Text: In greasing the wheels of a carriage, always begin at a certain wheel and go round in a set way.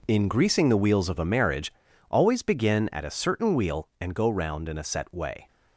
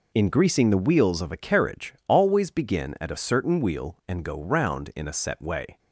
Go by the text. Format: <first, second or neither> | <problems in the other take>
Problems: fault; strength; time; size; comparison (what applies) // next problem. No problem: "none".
second | says "marriage" for "carriage"; at 1.2 s